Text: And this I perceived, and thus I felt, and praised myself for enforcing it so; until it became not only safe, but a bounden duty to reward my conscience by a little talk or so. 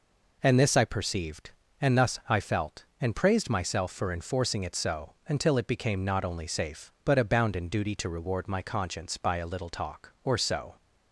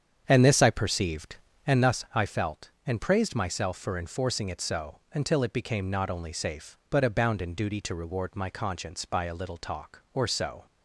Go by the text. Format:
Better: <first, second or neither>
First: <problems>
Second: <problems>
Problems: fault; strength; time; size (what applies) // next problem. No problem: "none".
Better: first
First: none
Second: starts louder than the rest; strong; until 2.0 s; 8 dB